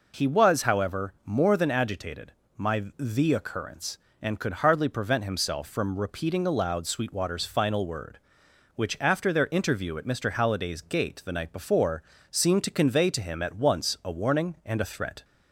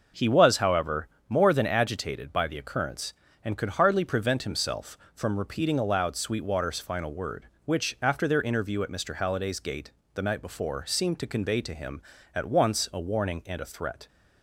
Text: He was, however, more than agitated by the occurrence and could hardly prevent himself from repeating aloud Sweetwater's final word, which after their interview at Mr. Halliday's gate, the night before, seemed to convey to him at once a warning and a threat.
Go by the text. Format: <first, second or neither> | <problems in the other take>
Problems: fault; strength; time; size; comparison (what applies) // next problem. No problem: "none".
second | says "my" for "by"; at 2.5 s